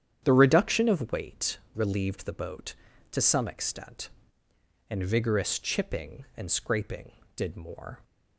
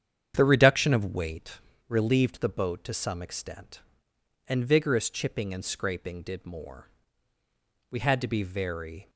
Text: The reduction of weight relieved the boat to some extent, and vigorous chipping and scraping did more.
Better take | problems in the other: first | starts louder than the rest; strong; until 1.3 s; 8.5 dB; strong in the first // pauses between "weight" and "relieved"; slight; at 1.5 s; 0.28 s long; slight in the first // goes on to say "We had to be very"; noticeable; from 7.8 s on; 1.2 s long

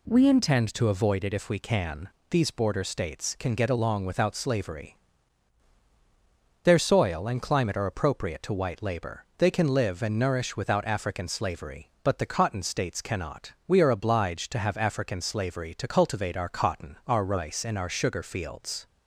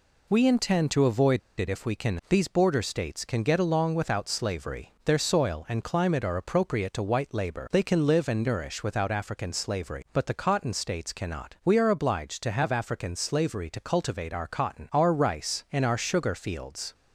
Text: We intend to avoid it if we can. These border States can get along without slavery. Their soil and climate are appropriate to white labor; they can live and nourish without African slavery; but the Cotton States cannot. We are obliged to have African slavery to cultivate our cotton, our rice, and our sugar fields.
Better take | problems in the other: first | pauses between "avoid" and "it"; slight; at 1.3 s; 0.19 s long

